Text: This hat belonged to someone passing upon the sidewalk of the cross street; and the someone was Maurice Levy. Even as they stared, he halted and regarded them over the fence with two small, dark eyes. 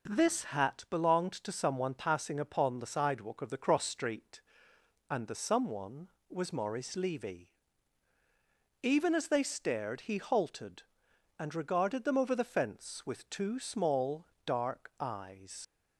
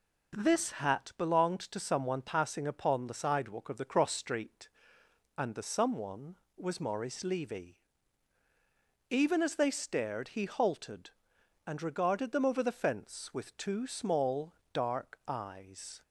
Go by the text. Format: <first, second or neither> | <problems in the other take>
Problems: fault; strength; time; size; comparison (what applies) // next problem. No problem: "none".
second | leaves "eyes" unfinished; at 15.6 s; 95 ms